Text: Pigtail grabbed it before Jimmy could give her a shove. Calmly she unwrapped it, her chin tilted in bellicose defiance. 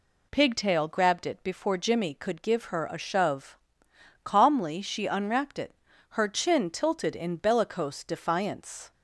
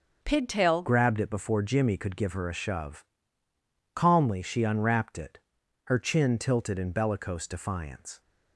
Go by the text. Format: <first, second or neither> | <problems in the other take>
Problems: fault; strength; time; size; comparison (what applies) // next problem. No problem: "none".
first | starts louder than the rest; until 1.2 s; 6.5 dB // changes voice at "grabbed"; from 0.8 s on; 7.4 s long